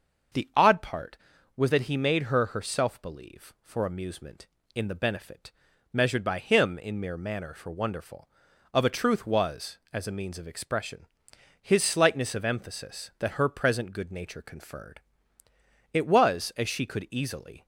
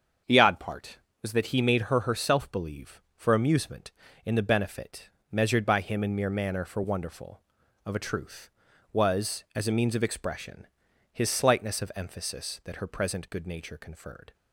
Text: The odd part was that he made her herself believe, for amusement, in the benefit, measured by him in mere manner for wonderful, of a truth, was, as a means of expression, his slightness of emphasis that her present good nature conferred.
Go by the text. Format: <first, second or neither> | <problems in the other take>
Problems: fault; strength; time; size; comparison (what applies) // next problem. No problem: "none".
second | starts louder than the rest; until 1.7 s; 6.5 dB; also in the second // goes on to say "It was as she could easily"; strong; from 15.9 s on; 1.7 s long